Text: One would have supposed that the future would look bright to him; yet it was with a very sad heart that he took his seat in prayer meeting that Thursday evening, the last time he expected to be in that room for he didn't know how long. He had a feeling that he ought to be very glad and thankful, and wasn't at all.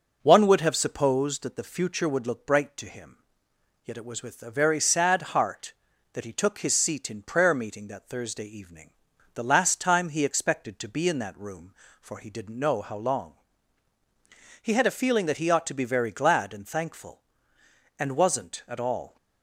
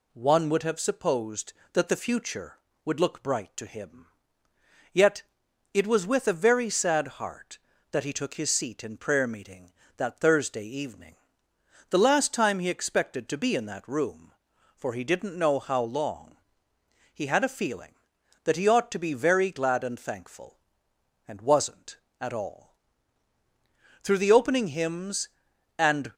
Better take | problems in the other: first | pauses between "yet" and "it"; noticeable; at 5.2 s; 0.50 s long // goes on to say "Through the opening hymns and"; strong; from 24.0 s on; 2.1 s long

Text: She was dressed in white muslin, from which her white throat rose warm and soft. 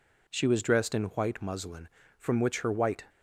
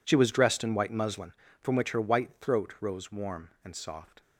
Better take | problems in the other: second | stops before "throat rose warm and soft"; at 3.0 s

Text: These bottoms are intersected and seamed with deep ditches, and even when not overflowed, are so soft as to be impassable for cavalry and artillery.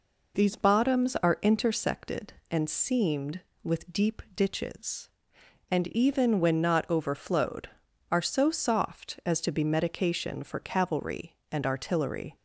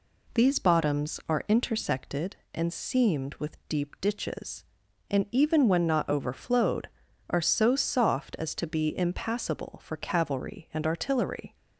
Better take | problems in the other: second | says "medication" for "impassable"; at 9.6 s

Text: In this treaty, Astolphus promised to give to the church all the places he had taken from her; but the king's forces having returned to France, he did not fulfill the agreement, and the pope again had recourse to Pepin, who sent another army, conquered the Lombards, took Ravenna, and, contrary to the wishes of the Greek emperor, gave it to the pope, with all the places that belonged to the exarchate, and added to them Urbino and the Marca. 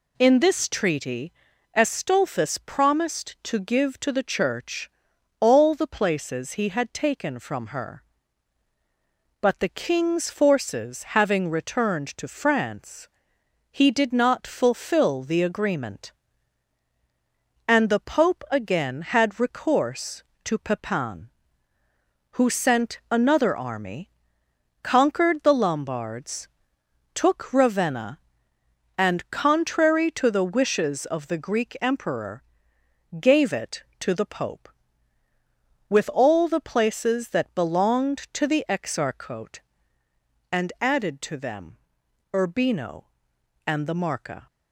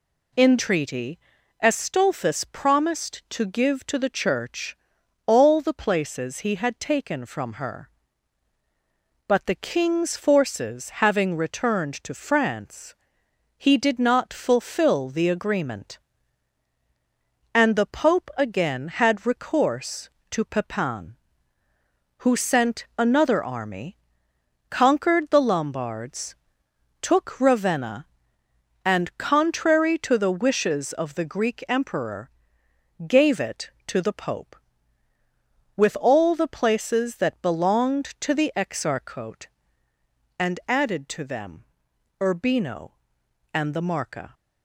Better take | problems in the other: first | skips "this"; at 0.5 s // pauses between "church" and "all"; noticeable; at 4.7 s; 0.52 s long; noticeable in the first // pauses between "them" and "Urbino"; noticeable; at 41.6 s; 0.56 s long; noticeable in the first

